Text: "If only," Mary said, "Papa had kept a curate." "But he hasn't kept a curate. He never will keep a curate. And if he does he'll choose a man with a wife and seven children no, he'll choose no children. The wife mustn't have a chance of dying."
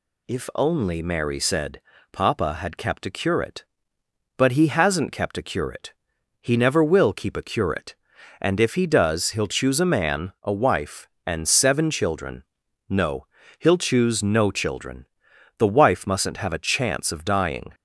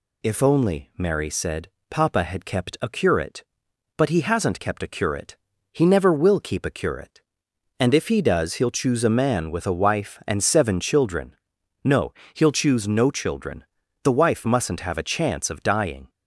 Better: second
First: skips "with"; at 10.3 s // pauses between "children" and "no"; noticeable; at 12.4 s; 0.46 s long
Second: pauses between "children" and "no"; noticeable; at 11.3 s; 0.48 s long

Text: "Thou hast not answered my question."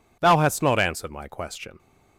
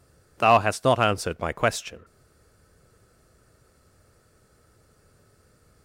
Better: first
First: none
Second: stays silent after the last word; strong; from 2.0 s on; 3.8 s long

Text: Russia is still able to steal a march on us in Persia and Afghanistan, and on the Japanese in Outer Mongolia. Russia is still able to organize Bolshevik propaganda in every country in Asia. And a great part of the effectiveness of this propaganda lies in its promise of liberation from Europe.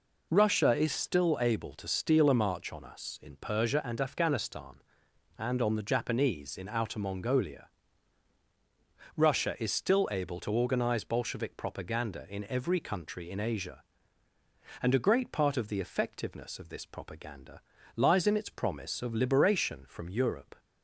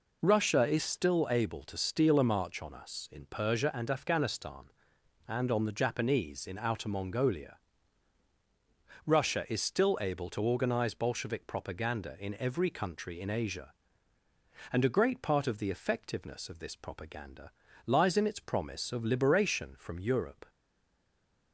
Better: first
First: pauses between "propaganda" and "lies"; slight; at 17.5 s; 0.36 s long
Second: pauses between "propaganda" and "lies"; slight; at 17.4 s; 0.36 s long // stays silent after the last word; from 20.4 s on; 1.1 s long

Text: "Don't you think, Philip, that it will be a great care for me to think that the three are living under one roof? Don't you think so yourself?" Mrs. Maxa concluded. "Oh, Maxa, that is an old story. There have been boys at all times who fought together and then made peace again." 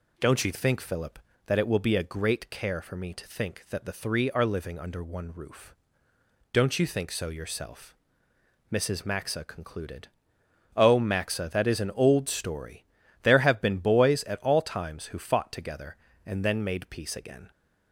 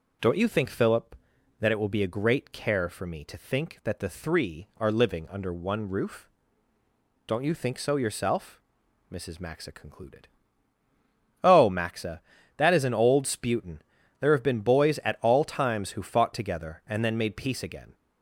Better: first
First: none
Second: says "sputin" for "story"; at 13.2 s

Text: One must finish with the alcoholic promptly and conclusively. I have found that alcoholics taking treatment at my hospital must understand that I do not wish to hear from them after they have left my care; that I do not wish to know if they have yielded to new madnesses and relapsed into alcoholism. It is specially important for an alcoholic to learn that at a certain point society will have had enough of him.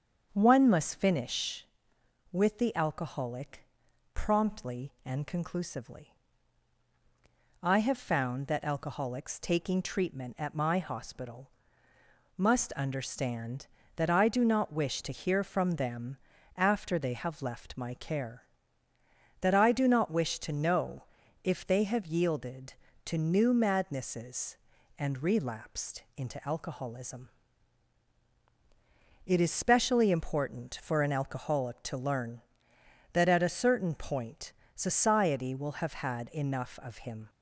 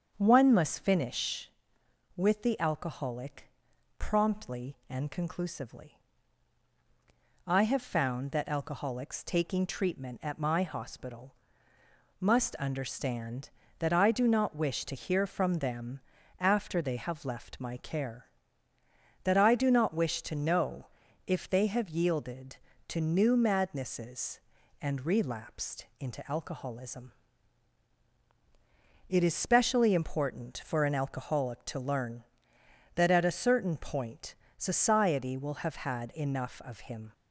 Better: neither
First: starts louder than the rest; until 1.3 s; 7 dB // pauses between "alcoholic" and "promptly"; noticeable; at 3.6 s; 0.50 s long // pauses between "hospital" and "must"; noticeable; at 11.5 s; 0.88 s long // pauses between "them" and "after"; at 16.1 s; 0.40 s long // pauses between "know" and "if"; at 21.0 s; 0.40 s long // pauses between "point" and "society"; slight; at 34.5 s; 0.22 s long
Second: starts louder than the rest; until 1.1 s; 7 dB // pauses between "alcoholic" and "promptly"; noticeable; at 3.4 s; 0.50 s long // pauses between "hospital" and "must"; noticeable; at 11.3 s; 0.86 s long // pauses between "them" and "after"; at 15.9 s; 0.40 s long // pauses between "know" and "if"; at 20.8 s; 0.40 s long // pauses between "point" and "society"; slight; at 34.3 s; 0.22 s long

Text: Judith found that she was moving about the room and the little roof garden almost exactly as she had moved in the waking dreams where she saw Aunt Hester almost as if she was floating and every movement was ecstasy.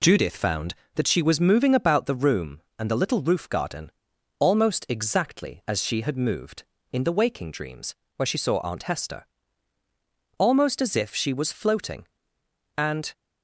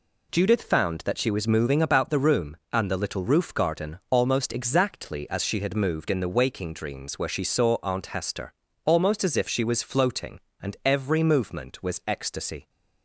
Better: second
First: pauses between "garden" and "almost"; noticeable; at 3.8 s; 0.52 s long // pauses between "dreams" and "where"; slight; at 7.9 s; 0.22 s long // pauses between "Hester" and "almost"; at 9.2 s; 1.1 s long // stops before "every movement was ecstasy"; at 13.1 s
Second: pauses between "Hester" and "almost"; slight; at 8.5 s; 0.32 s long

